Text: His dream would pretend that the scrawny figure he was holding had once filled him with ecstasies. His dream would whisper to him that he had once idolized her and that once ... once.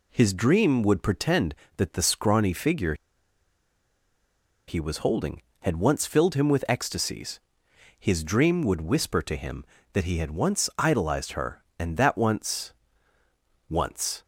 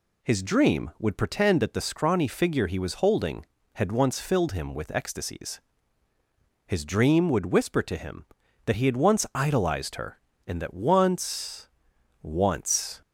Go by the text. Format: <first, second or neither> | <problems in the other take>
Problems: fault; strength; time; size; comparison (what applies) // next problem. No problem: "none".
second | pauses between "figure" and "he"; strong; at 2.9 s; 1.7 s long